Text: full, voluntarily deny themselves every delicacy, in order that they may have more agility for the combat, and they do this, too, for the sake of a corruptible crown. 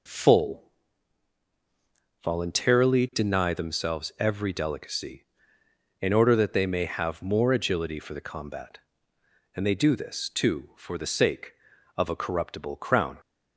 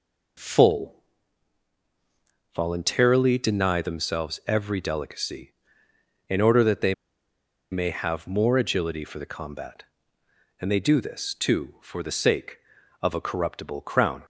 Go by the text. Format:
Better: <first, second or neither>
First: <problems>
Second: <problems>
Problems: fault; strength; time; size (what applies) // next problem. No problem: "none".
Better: first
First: none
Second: pauses between "they" and "may"; noticeable; at 6.9 s; 0.77 s long